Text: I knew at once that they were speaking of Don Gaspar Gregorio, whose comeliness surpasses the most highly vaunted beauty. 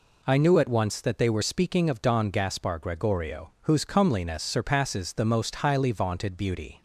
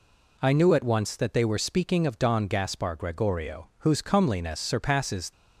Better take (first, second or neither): first